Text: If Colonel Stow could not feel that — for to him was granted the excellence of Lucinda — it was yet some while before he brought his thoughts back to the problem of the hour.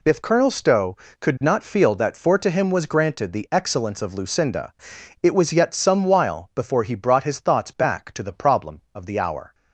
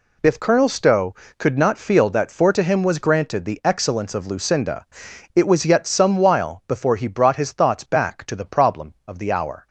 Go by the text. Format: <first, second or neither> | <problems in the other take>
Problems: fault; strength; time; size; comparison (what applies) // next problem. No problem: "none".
neither | none